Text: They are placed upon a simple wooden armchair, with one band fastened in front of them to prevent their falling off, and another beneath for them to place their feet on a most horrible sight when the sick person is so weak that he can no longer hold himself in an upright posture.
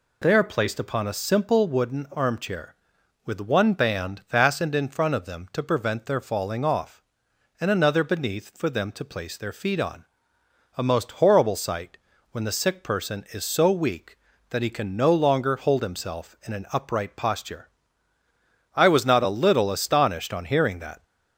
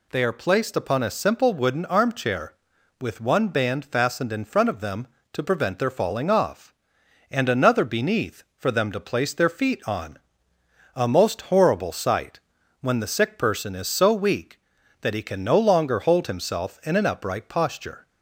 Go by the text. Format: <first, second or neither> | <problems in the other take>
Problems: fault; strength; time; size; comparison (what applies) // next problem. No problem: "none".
second | pauses between "on" and "a"; noticeable; at 10.0 s; 0.72 s long; noticeable in the second // pauses between "sight" and "when"; slight; at 11.9 s; 0.34 s long; also in the second // goes on to say "I was not a little astonished on hearing that"; strong; from 18.7 s on; 2.2 s long